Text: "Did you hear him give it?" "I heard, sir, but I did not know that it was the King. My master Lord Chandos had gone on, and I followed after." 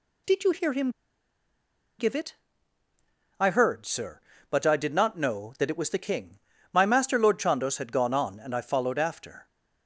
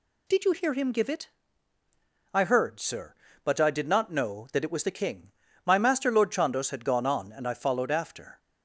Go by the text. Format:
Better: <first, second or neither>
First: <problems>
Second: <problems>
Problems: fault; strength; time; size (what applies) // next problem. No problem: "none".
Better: second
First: pauses between "him" and "give"; at 0.8 s; 1.0 s long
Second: none